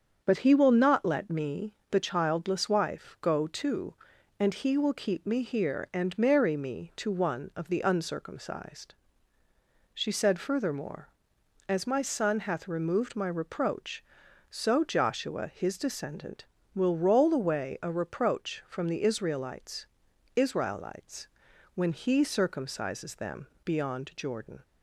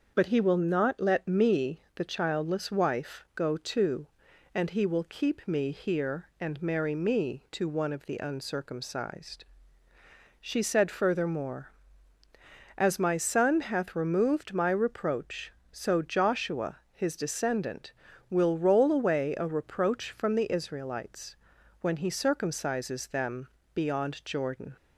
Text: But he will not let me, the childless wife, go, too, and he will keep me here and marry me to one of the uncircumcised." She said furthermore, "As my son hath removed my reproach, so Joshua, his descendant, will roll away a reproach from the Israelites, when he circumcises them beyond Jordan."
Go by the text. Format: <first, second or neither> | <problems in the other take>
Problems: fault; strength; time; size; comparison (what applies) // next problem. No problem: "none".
second | starts louder than the rest; strong; until 1.2 s; 7 dB; noticeable in the second // says "Israelites" twice; at 20.3 s // pauses between "them" and "beyond"; slight; at 23.4 s; 0.18 s long; slight in the second